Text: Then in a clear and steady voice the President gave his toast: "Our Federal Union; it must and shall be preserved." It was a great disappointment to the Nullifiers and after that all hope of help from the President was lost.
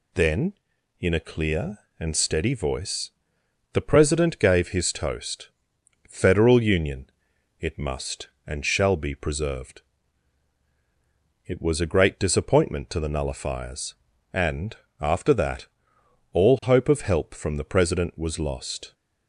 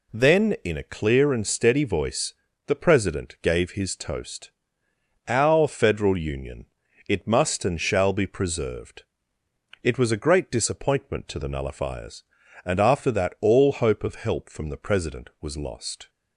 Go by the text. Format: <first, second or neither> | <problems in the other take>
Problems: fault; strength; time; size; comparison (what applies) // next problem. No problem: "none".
second | pauses between "voice" and "the"; noticeable; at 3.1 s; 0.62 s long; slight in the second // skips "Our"; at 5.7 s // pauses between "and" and "after"; slight; at 14.7 s; 0.24 s long // pauses between "that" and "all"; noticeable; at 15.6 s; 0.66 s long